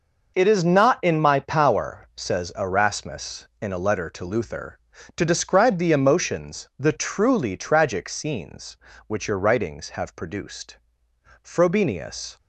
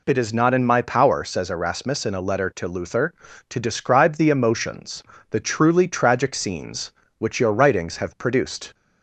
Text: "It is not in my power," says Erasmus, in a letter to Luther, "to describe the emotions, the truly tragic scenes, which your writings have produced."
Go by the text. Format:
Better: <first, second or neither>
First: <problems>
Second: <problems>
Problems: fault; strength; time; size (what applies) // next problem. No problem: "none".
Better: second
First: goes on to say "Frobenius"; noticeable; from 11.4 s on; 0.94 s long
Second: none